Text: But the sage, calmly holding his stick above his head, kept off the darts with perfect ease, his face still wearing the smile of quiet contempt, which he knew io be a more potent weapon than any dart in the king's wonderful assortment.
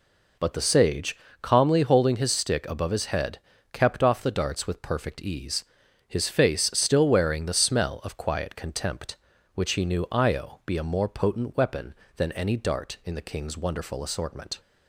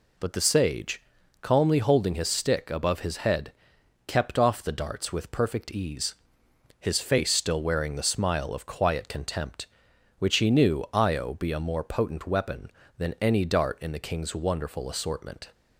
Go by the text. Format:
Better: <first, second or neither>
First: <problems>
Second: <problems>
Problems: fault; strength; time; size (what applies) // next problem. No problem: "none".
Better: second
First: says "smell" for "smile"; at 7.5 s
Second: none